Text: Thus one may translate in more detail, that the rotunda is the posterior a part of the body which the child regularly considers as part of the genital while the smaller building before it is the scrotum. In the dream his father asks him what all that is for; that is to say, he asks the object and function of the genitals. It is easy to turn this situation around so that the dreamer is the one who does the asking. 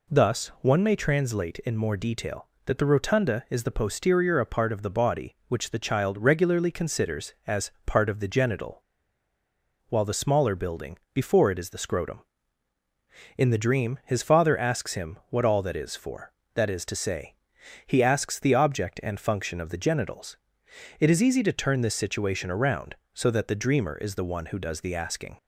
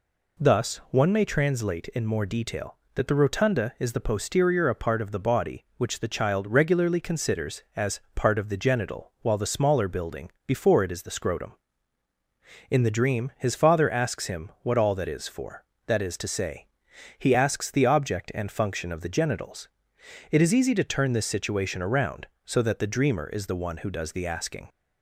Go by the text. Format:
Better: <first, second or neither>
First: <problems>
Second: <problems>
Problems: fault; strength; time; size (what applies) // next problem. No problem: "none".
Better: second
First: pauses between "genital" and "while"; at 8.8 s; 1.0 s long // pauses between "building" and "before"; slight; at 10.9 s; 0.16 s long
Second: pauses between "building" and "before"; slight; at 10.2 s; 0.16 s long